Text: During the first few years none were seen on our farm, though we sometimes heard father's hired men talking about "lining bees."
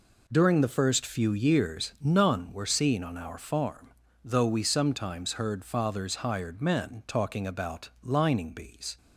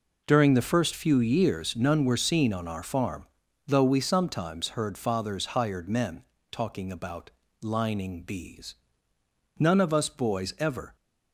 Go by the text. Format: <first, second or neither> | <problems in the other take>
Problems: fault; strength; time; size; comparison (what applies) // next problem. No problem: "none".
first | pauses between "men" and "talking"; slight; at 6.2 s; 0.26 s long // pauses between "about" and "lining"; slight; at 7.2 s; 0.32 s long // goes on to say "None of us boys ever"; from 9.5 s on; 1.3 s long